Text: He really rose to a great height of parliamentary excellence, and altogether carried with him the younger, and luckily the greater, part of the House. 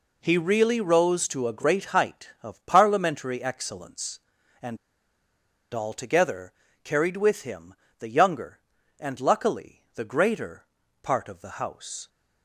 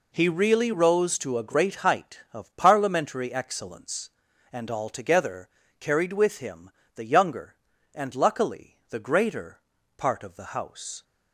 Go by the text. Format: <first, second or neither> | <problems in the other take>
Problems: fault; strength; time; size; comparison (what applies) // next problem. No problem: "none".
second | pauses between "and" and "altogether"; noticeable; at 4.7 s; 0.96 s long // pauses between "altogether" and "carried"; slight; at 6.5 s; 0.32 s long; slight in the second // pauses between "him" and "the"; slight; at 7.7 s; 0.28 s long; slight in the second